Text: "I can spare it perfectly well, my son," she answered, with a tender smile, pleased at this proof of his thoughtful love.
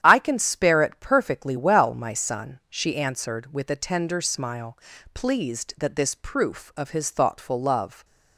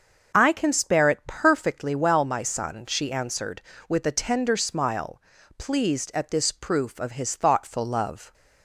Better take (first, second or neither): second